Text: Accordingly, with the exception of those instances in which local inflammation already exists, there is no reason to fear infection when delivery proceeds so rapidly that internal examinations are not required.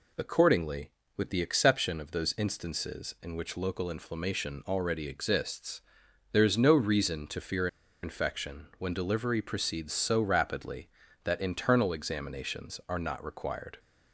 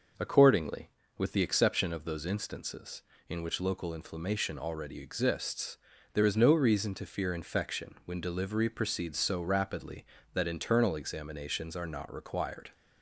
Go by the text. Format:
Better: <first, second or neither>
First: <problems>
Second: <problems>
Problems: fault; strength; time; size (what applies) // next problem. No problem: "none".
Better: second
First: pauses between "fear" and "infection"; slight; at 7.6 s; 0.35 s long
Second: none